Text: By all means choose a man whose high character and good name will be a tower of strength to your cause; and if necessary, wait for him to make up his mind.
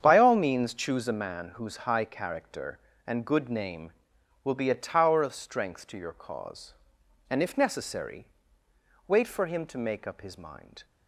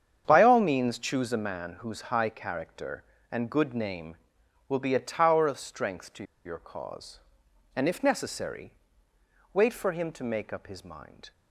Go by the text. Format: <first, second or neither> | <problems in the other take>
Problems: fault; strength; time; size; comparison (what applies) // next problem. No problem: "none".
first | starts louder than the rest; strong; until 1.2 s; 8 dB; strong in the first // pauses between "to" and "your"; slight; at 6.2 s; 0.21 s long